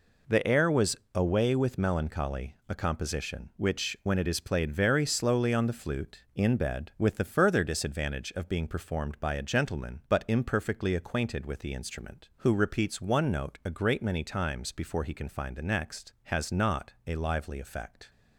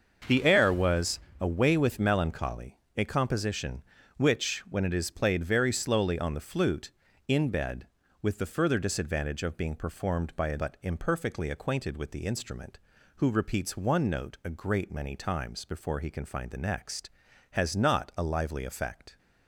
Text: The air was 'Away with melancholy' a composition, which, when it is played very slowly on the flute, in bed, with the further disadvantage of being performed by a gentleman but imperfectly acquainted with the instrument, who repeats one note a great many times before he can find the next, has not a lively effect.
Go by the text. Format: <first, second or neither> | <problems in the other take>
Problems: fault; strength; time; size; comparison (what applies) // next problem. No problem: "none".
first | starts louder than the rest; until 1.5 s; 6.5 dB // pauses between "was" and "Away"; slight; at 1.1 s; 0.22 s long; slight in the first // pauses between "melancholy" and "a"; slight; at 2.7 s; 0.16 s long // skips "gentleman"; at 10.5 s